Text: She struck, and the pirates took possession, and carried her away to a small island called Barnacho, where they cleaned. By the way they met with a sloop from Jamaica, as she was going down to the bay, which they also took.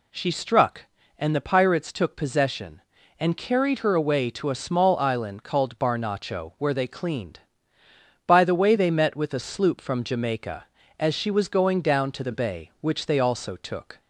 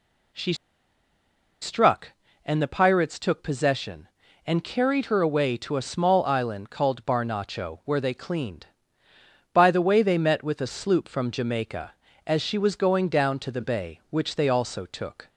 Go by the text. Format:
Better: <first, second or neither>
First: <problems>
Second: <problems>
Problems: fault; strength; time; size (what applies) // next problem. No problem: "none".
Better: first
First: none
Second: pauses between "She" and "struck"; at 0.5 s; 1.0 s long